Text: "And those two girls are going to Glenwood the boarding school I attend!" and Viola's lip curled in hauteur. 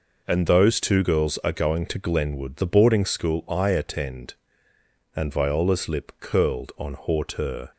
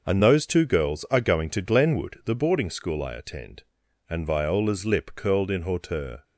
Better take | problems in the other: second | says "on" for "in"; at 6.7 s

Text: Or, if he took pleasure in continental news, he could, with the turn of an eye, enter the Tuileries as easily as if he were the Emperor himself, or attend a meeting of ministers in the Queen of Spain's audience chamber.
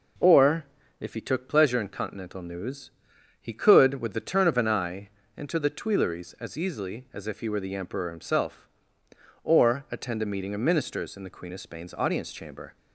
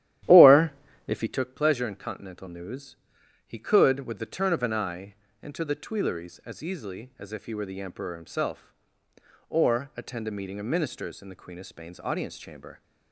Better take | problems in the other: first | starts louder than the rest; strong; until 1.4 s; 12 dB

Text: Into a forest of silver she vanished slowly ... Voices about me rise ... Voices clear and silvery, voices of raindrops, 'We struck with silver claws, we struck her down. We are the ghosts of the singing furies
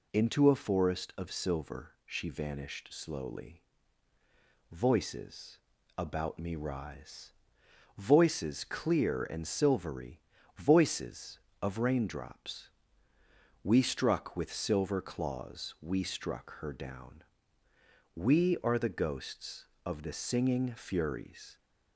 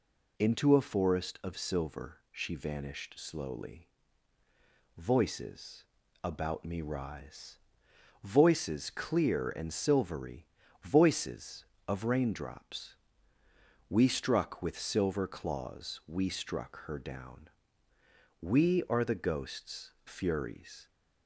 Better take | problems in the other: first | pauses between "Voices" and "about"; at 5.8 s; 0.38 s long; also in the first // skips "of the singing"; at 19.9 s

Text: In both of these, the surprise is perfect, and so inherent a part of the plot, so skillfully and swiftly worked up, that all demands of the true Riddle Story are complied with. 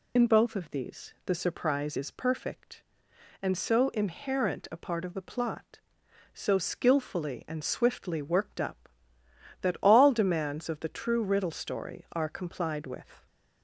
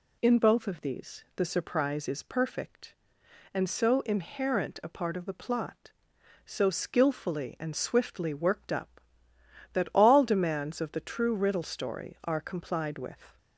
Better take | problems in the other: second | loses the start of "In"; at 0.1 s; 70 ms

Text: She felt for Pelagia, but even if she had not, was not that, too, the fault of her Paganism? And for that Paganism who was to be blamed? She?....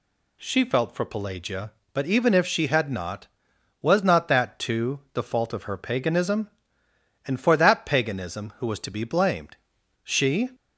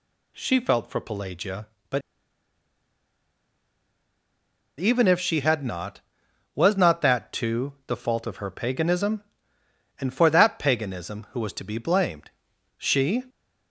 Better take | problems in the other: first | pauses between "but" and "even"; strong; at 2.0 s; 2.7 s long

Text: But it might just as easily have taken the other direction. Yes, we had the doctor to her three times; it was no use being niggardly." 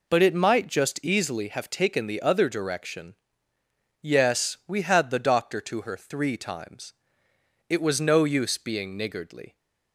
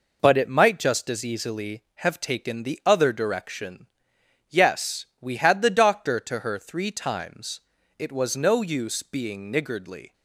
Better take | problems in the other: second | skips "as"; at 1.0 s

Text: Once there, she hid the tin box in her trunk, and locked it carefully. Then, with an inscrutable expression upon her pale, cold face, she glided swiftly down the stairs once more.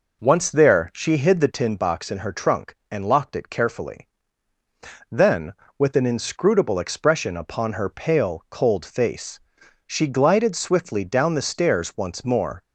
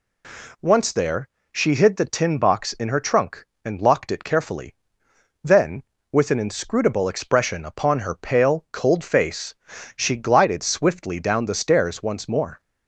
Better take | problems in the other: second | starts louder than the rest; noticeable; until 1.9 s; 5 dB

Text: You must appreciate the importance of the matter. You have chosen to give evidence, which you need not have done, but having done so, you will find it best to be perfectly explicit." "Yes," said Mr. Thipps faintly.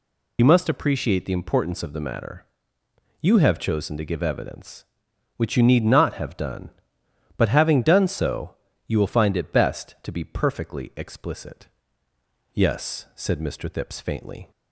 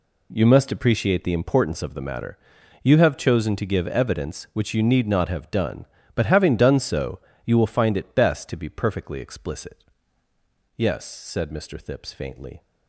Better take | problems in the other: second | loses the start of "You"; at 0.3 s; 35 ms

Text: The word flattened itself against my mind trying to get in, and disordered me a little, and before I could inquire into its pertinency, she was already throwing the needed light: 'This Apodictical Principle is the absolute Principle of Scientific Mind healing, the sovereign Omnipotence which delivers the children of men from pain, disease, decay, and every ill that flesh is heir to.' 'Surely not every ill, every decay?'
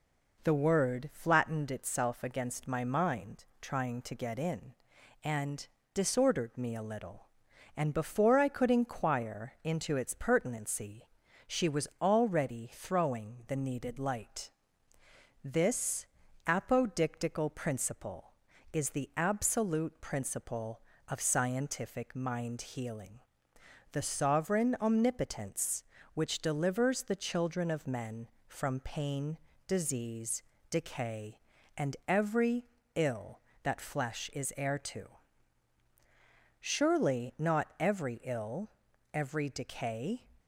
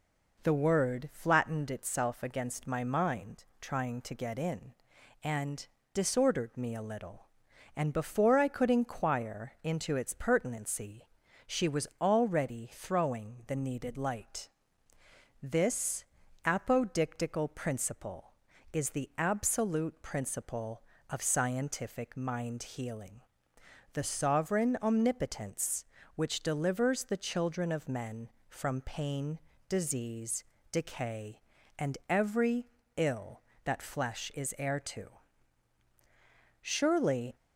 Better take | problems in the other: first | pauses between "mind" and "trying"; slight; at 3.4 s; 0.16 s long; slight in the first // pauses between "and" and "disordered"; slight; at 5.6 s; 0.26 s long; slight in the first // pauses between "This" and "Apodictical"; at 16.0 s; 0.40 s long; also in the first // pauses between "every" and "ill"; slight; at 32.6 s; 0.30 s long; slight in the first // stops before "not every ill every decay"; at 37.3 s

